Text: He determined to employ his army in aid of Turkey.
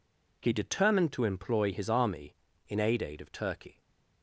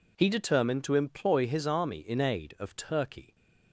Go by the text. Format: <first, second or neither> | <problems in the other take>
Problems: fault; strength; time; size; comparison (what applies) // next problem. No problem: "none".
second | says "aid" twice; at 3.0 s // stays silent after the last word; slight; from 3.7 s on; 0.5 s long